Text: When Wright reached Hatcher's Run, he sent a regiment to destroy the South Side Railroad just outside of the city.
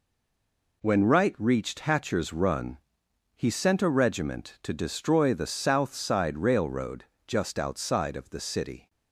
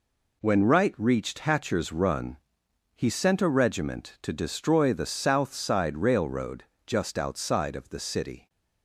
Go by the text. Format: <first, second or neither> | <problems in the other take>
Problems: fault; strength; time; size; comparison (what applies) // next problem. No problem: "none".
second | stays silent before the first word; slight; until 0.8 s; 0.8 s long // pauses between "Railroad" and "just"; slight; at 7.0 s; 0.24 s long; slight in the second